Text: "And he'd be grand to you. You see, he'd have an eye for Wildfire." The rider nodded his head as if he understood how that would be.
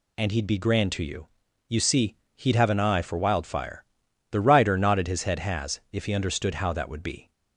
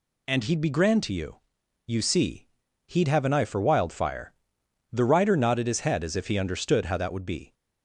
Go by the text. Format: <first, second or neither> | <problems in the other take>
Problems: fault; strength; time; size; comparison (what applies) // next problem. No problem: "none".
second | says "has" for "as"; at 5.3 s